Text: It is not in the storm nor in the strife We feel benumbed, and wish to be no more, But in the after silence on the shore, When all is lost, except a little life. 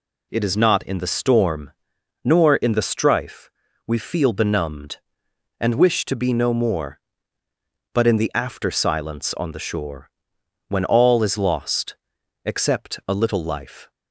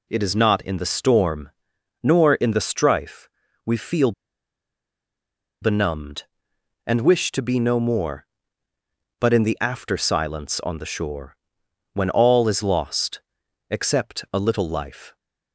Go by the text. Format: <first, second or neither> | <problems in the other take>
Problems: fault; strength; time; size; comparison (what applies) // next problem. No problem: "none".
first | pauses between "storm" and "nor"; noticeable; at 1.4 s; 0.52 s long; noticeable in the first // pauses between "strife" and "We"; at 3.2 s; 0.38 s long; also in the first // pauses between "feel" and "benumbed"; strong; at 4.1 s; 1.5 s long